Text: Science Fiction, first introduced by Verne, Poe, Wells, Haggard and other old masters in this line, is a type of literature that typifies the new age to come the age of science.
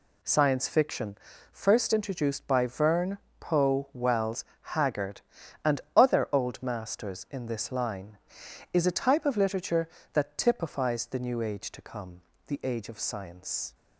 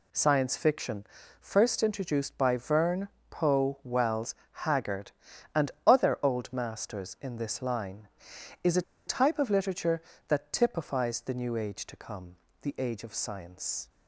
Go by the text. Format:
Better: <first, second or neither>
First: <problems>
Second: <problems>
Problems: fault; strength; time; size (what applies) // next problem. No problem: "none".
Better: first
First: pauses between "and" and "other"; slight; at 5.7 s; 0.16 s long // pauses between "come" and "the"; slight; at 12.2 s; 0.26 s long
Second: pauses between "and" and "other"; slight; at 5.7 s; 0.16 s long // pauses between "a" and "type"; slight; at 8.8 s; 0.24 s long // pauses between "come" and "the"; slight; at 12.3 s; 0.26 s long